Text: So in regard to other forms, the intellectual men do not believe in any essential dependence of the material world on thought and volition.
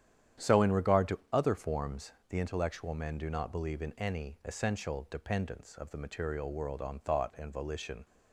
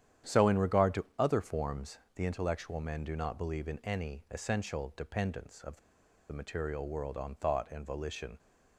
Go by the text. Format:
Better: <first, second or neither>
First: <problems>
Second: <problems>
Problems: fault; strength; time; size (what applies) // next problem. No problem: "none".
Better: first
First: starts louder than the rest; strong; until 1.5 s; 10 dB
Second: starts louder than the rest; strong; until 1.4 s; 10 dB // pauses between "the" and "material"; noticeable; at 5.7 s; 0.52 s long